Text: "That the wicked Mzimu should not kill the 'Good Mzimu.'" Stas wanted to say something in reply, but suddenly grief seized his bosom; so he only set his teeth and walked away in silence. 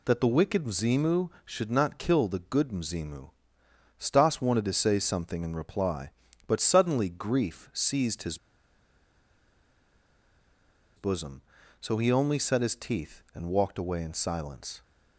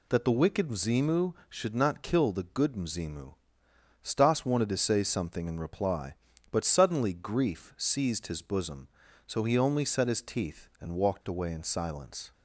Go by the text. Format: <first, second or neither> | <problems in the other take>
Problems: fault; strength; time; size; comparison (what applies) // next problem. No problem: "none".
second | pauses between "his" and "bosom"; strong; at 8.3 s; 2.6 s long